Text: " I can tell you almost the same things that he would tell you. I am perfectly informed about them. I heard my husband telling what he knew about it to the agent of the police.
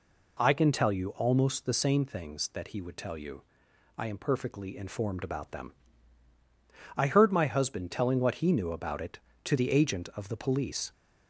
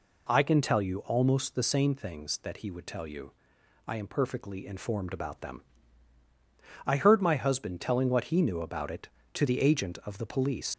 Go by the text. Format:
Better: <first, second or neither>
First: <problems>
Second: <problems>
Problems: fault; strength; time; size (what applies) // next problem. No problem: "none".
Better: first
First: none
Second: leaves "police" unfinished; at 10.7 s; 75 ms